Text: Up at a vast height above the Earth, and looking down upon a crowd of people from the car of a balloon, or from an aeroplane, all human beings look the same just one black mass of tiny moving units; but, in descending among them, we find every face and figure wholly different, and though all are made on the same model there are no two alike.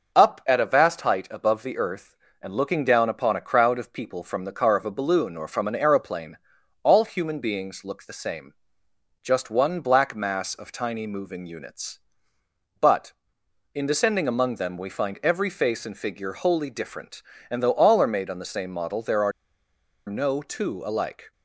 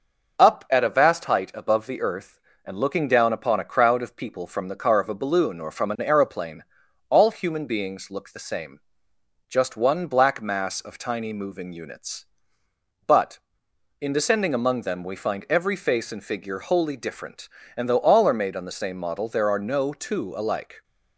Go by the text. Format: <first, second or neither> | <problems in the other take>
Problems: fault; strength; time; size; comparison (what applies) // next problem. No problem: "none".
second | starts louder than the rest; noticeable; until 1.1 s; 6 dB; noticeable in the second // pauses between "same" and "just"; noticeable; at 8.5 s; 0.70 s long; noticeable in the second // pauses between "are" and "no"; noticeable; at 19.3 s; 0.76 s long